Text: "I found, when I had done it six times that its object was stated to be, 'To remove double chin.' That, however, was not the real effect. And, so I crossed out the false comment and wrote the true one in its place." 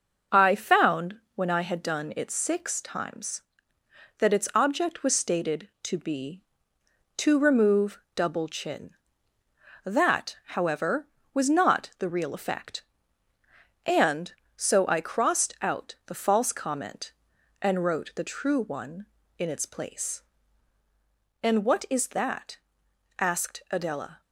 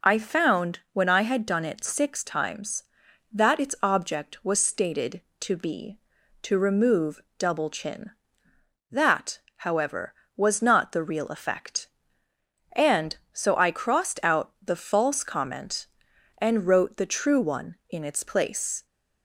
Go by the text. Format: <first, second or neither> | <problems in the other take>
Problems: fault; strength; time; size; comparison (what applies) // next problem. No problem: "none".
second | starts louder than the rest; noticeable; until 1.4 s; 6 dB // pauses between "remove" and "double"; slight; at 7.9 s; 0.16 s long; slight in the second // goes on to say "And what is that asked Adela"; strong; from 21.4 s on; 2.7 s long